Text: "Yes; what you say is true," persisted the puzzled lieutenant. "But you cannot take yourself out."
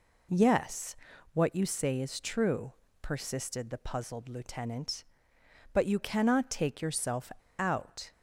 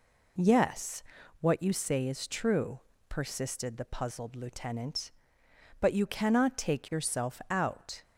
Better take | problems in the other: second | pauses between "yourself" and "out"; slight; at 7.3 s; 0.27 s long

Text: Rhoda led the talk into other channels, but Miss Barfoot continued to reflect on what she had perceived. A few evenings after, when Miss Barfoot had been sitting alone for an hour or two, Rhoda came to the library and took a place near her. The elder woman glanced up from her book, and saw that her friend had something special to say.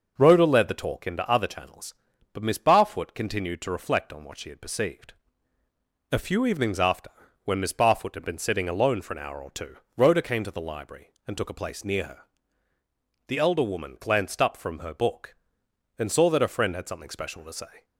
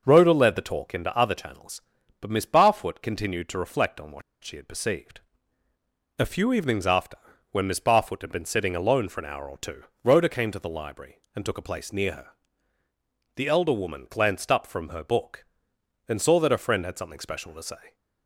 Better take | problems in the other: first | pauses between "what" and "she"; slight; at 4.2 s; 0.22 s long

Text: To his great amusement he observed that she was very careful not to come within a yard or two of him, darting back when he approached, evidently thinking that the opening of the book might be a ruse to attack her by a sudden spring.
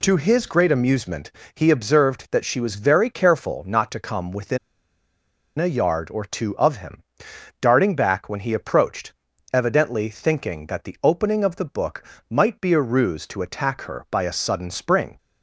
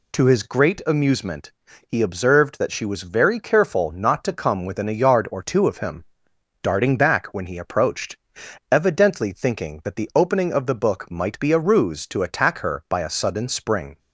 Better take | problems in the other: second | pauses between "amusement" and "he"; slight; at 1.2 s; 0.24 s long; slight in the second // pauses between "within" and "a"; at 4.5 s; 1.0 s long // pauses between "book" and "might"; slight; at 12.0 s; 0.24 s long

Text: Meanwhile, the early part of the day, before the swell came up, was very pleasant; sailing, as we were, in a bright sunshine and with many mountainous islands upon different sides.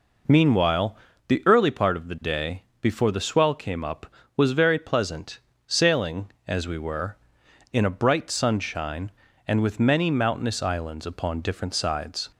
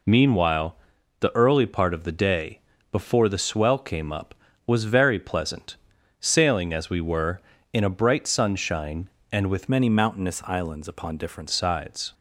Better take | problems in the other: first | changes voice from "many" to "different"; from 9.6 to 11.4 s; 1.8 s long

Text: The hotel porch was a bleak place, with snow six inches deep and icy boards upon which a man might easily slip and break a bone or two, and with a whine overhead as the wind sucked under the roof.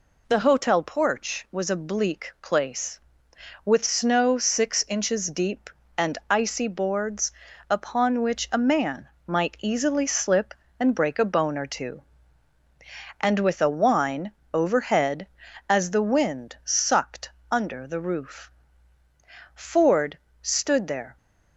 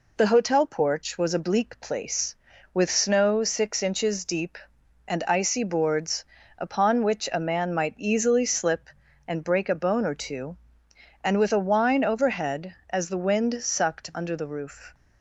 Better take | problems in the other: second | pauses between "boards" and "upon"; at 7.3 s; 0.38 s long; slight in the second // pauses between "man" and "might"; slight; at 9.0 s; 0.20 s long // pauses between "whine" and "overhead"; slight; at 14.3 s; 0.20 s long // pauses between "sucked" and "under"; slight; at 17.2 s; 0.22 s long // goes on to say "Ford stood there"; from 19.5 s on; 1.6 s long

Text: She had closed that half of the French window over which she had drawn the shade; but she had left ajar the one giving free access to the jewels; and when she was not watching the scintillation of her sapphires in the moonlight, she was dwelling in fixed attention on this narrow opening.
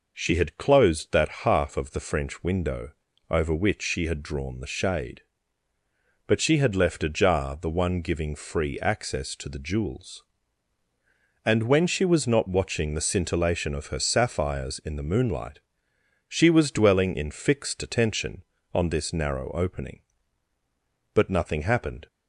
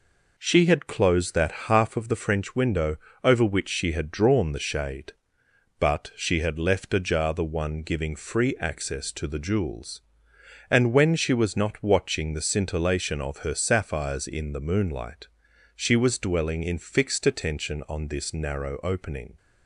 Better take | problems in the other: second | pauses between "window" and "over"; slight; at 2.9 s; 0.36 s long; slight in the second // goes on to say "But nothing happened"; noticeable; from 21.1 s on; 0.94 s long

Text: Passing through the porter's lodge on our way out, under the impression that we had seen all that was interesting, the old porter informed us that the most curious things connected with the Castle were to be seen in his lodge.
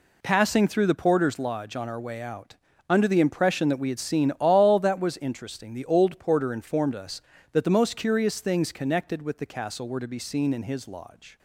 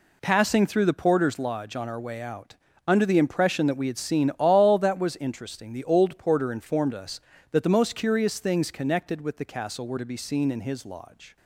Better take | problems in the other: neither | none

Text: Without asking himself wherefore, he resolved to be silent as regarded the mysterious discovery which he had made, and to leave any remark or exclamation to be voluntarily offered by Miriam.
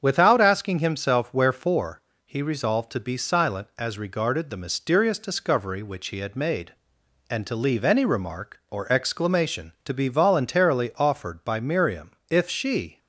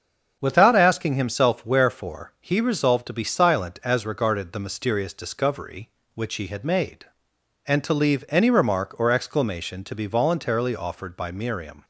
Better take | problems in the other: second | starts louder than the rest; strong; until 1.0 s; 7.5 dB; also in the second // goes on to say "If she"; noticeable; from 12.2 s on; 0.70 s long

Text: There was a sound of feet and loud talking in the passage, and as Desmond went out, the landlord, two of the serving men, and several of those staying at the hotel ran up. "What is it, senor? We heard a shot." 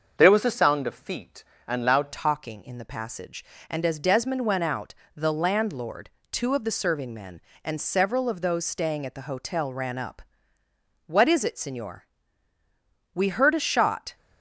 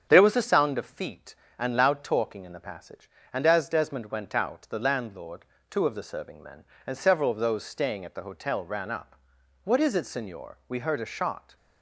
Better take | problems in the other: second | starts louder than the rest; until 1.1 s; 6.5 dB; strong in the second // changes voice at "talking"; from 2.1 s on; 12.0 s long

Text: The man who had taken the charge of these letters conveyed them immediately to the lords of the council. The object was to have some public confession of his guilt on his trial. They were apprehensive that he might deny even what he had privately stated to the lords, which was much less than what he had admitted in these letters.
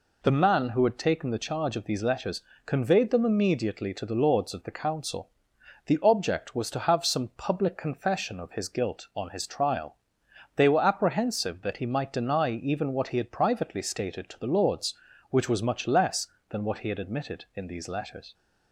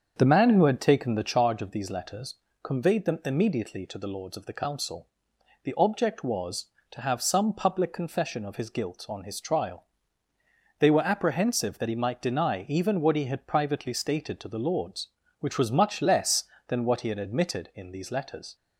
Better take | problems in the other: first | starts louder than the rest; until 1.4 s; 7 dB // pauses between "letters" and "conveyed"; slight; at 2.3 s; 0.28 s long; slight in the first

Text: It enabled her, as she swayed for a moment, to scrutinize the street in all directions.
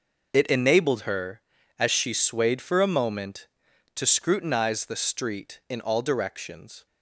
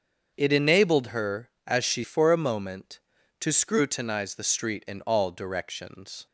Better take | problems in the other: first | starts louder than the rest; until 1.3 s; 7 dB // skips "swayed"; at 2.0 s

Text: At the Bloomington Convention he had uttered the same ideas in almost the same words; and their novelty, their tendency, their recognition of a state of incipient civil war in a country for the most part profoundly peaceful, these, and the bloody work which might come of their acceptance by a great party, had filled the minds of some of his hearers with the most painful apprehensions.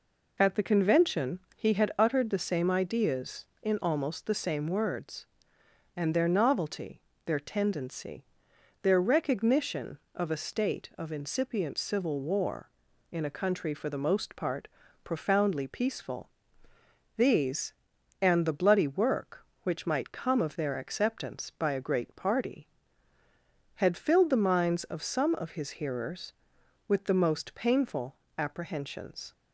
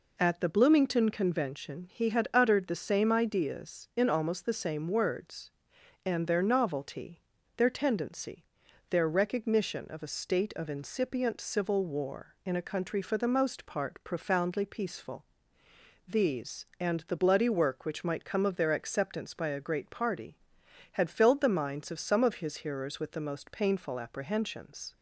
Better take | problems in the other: second | skips "Bloomington"; at 0.6 s // pauses between "Convention" and "he"; slight; at 1.3 s; 0.16 s long // pauses between "part" and "profoundly"; slight; at 14.6 s; 0.36 s long // pauses between "painful" and "apprehensions"; slight; at 28.1 s; 0.20 s long

